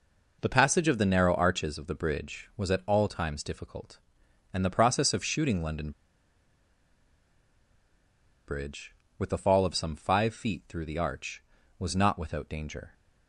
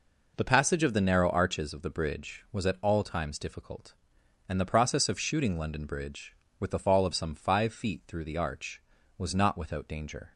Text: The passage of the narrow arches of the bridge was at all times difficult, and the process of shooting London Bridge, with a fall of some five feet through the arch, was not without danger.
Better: second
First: pauses between "London" and "Bridge"; strong; at 5.9 s; 2.5 s long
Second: none

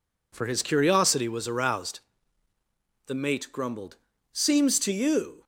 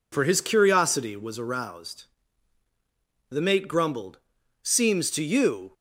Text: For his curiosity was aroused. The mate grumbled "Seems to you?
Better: neither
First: pauses between "grumbled" and "Seems"; slight; at 3.9 s; 0.36 s long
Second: pauses between "grumbled" and "Seems"; at 4.1 s; 0.42 s long

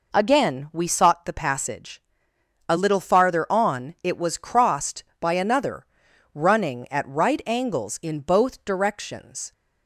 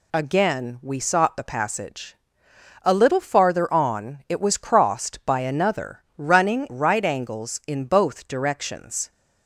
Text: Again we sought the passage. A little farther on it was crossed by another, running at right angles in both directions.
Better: first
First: none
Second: skips "at"; at 6.6 s

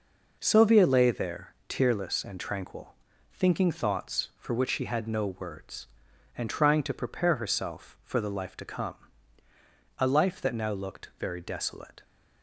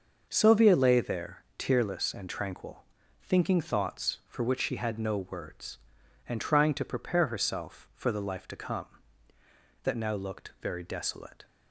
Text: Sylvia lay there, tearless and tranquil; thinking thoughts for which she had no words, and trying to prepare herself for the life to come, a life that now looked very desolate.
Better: first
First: none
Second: starts louder than the rest; noticeable; until 1.3 s; 6 dB // skips "a life"; at 9.3 s

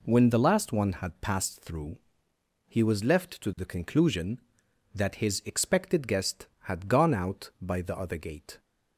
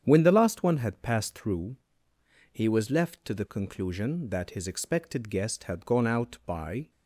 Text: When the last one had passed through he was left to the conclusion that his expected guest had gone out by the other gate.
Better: first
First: pauses between "through" and "he"; noticeable; at 1.9 s; 0.70 s long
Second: starts louder than the rest; strong; until 1.0 s; 8.5 dB // pauses between "through" and "he"; noticeable; at 1.7 s; 0.76 s long // stops before "the other gate"; at 6.8 s

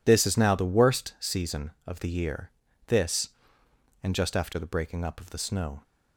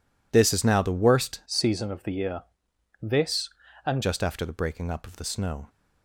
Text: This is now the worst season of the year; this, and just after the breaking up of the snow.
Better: first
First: none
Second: changes voice from "season" to "and"; from 1.4 to 4.0 s; 2.6 s long

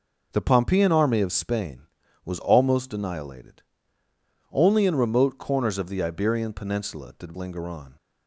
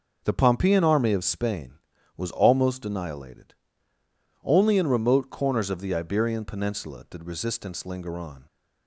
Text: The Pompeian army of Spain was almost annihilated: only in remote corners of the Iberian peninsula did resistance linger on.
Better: second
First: skips "resistance"; at 7.3 s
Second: none

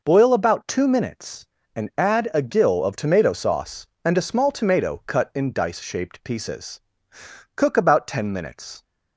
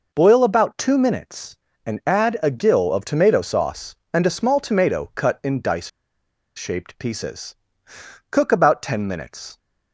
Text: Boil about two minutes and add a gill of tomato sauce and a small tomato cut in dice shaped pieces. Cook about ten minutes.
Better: first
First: none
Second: pauses between "dice" and "shaped"; noticeable; at 5.8 s; 0.68 s long

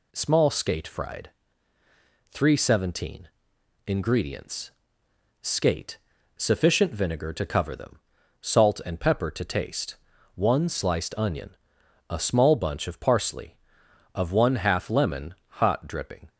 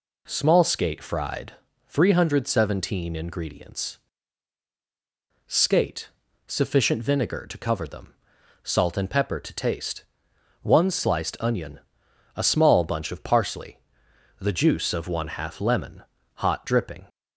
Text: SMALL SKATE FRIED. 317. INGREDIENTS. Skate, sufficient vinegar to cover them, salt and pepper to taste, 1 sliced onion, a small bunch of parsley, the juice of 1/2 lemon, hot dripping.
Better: second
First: skips "the juice"; at 13.8 s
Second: none

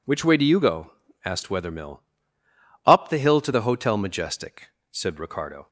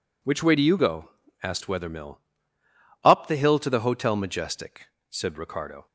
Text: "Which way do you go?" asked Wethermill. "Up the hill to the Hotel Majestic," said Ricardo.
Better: neither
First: none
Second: none

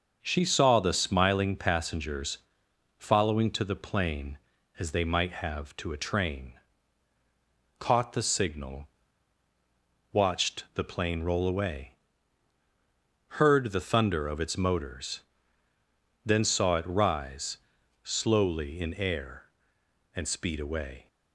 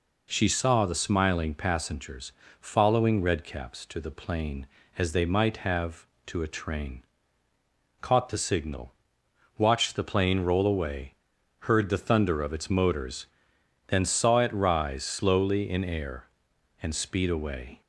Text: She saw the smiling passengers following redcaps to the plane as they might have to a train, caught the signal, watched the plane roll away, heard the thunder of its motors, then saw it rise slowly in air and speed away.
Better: second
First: pauses between "passengers" and "following"; noticeable; at 2.3 s; 0.60 s long // skips "redcaps"; at 3.5 s // pauses between "rise" and "slowly"; noticeable; at 17.5 s; 0.46 s long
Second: pauses between "passengers" and "following"; slight; at 2.3 s; 0.28 s long

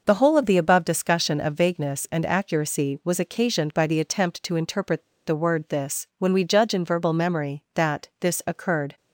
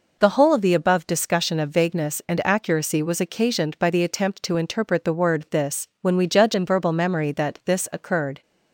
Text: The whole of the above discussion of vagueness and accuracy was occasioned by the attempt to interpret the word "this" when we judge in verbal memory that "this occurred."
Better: second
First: pauses between "interpret" and "the"; slight; at 4.9 s; 0.27 s long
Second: none

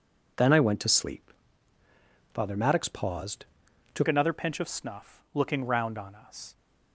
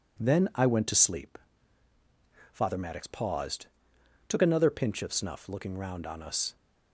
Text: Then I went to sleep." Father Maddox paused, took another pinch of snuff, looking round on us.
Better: second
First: changes voice at "another"; from 4.0 s on; 2.5 s long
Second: none

